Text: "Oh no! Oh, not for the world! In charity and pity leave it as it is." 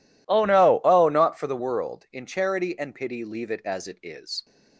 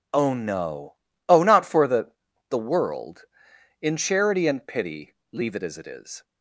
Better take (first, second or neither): first